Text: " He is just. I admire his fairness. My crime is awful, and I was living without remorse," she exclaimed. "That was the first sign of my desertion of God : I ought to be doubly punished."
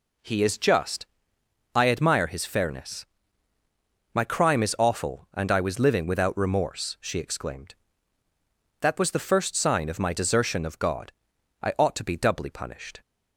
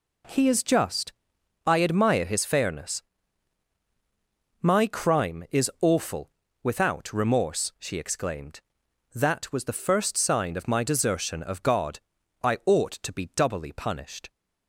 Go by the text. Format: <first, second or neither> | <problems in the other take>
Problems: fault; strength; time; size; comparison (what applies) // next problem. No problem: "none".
first | skips "and I was living"; at 6.4 s